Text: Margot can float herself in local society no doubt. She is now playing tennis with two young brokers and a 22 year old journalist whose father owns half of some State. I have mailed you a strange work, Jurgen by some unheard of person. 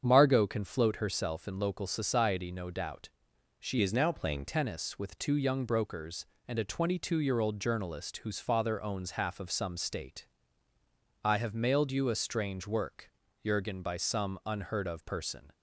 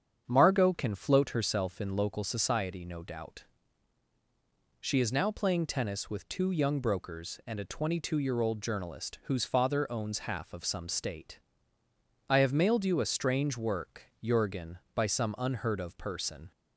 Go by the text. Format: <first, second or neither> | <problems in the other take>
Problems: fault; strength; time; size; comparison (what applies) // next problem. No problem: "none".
second | starts louder than the rest; strong; until 1.0 s; 7.5 dB; strong in the second // changes voice from "is" to "playing"; from 3.8 to 4.4 s; 0.6 s long